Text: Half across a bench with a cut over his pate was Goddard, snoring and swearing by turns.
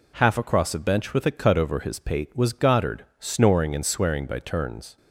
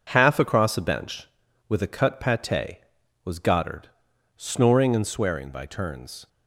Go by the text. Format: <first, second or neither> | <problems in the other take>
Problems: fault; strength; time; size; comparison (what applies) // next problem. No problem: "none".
first | skips "over his"; at 2.1 s